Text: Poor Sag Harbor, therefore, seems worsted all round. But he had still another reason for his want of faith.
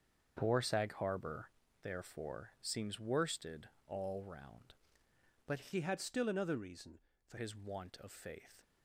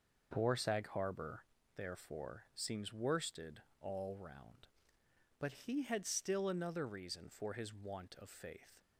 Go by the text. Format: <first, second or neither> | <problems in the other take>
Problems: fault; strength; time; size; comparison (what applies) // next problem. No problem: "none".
second | starts louder than the rest; until 1.4 s; 6.5 dB // pauses between "worsted" and "all"; slight; at 3.6 s; 0.22 s long; slight in the second // changes voice from "he" to "for"; from 5.7 to 7.3 s; 1.6 s long